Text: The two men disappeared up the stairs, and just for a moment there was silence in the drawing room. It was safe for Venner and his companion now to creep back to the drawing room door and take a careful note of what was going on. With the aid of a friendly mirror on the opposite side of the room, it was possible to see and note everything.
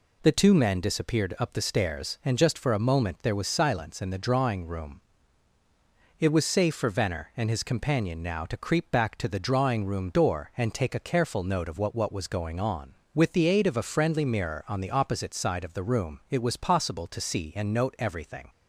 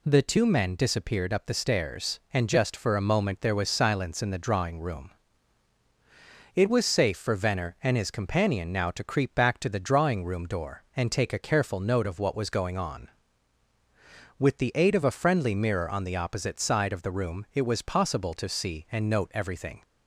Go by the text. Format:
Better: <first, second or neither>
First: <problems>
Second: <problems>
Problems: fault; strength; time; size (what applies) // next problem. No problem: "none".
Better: second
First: says "what" twice; at 11.9 s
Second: none